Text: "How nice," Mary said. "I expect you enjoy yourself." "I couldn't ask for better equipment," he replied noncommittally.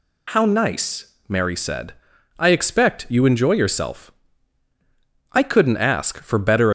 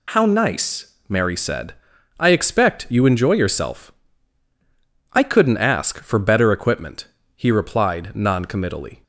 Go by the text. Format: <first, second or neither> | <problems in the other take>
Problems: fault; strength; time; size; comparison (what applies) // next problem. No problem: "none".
second | stops before "equipment he replied noncommittally"; at 6.6 s